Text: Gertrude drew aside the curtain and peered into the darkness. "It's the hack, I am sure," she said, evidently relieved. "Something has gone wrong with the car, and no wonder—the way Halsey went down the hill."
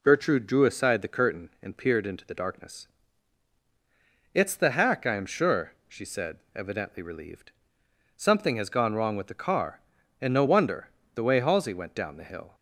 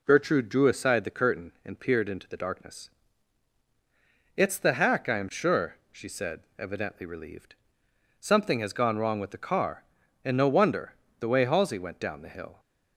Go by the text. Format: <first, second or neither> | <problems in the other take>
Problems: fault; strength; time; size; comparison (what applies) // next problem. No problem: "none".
neither | none